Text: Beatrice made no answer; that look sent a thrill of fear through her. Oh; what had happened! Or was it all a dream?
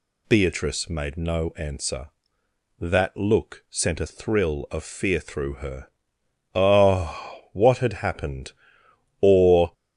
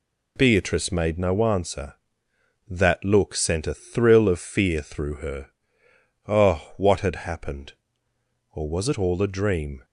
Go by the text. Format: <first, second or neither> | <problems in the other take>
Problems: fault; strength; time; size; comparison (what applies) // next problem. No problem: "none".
second | stops before "was it all a dream"; at 9.7 s